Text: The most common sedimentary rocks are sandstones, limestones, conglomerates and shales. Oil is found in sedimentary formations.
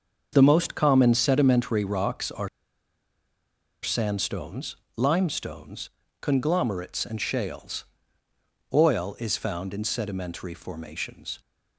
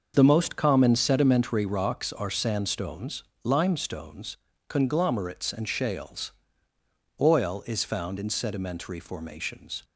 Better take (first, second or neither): second